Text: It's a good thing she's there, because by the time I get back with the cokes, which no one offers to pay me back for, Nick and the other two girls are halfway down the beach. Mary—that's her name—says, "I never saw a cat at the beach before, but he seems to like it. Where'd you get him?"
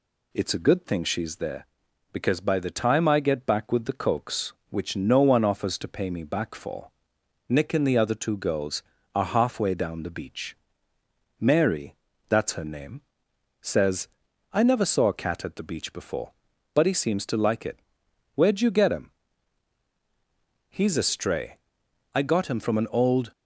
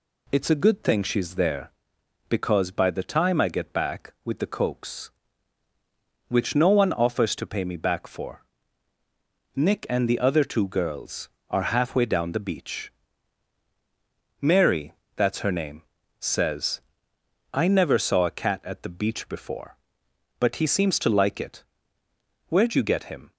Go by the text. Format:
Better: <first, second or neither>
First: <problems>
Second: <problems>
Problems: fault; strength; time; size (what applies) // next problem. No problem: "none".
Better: second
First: goes on to say "He's a stray I got him from an old"; strong; from 20.6 s on; 2.6 s long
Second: none